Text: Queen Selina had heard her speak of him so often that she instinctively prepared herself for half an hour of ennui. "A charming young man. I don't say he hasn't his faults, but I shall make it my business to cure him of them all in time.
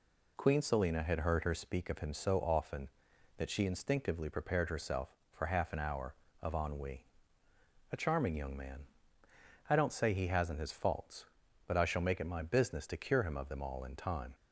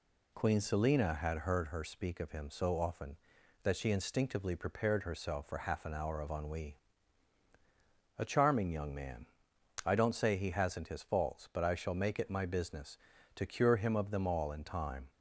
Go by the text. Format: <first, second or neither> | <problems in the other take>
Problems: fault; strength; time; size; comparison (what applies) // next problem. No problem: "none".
neither | none